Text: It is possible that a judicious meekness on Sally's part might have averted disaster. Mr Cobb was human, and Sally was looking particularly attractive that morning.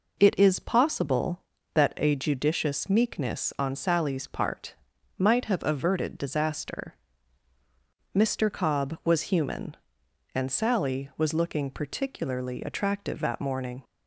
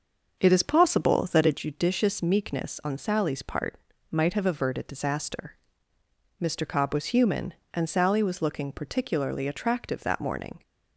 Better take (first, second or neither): first